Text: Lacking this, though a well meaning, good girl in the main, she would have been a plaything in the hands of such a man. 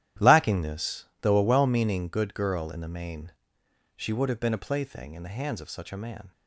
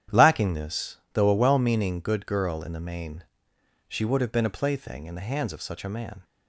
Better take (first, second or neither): second